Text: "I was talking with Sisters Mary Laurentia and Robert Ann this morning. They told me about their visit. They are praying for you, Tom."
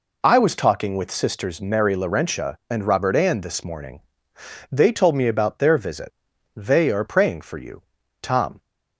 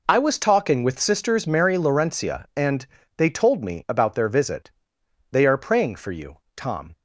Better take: first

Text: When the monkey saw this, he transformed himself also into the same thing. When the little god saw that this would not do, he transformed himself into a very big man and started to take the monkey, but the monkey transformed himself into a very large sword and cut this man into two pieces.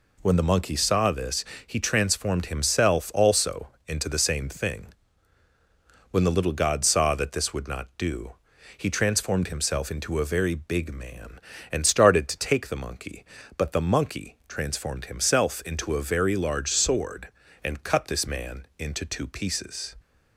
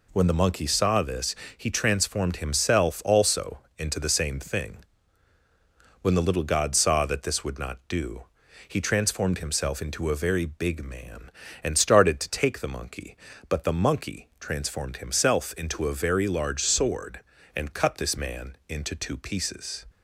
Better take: neither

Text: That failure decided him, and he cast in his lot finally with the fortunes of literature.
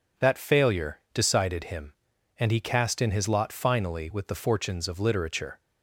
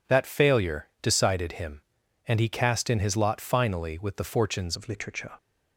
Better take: first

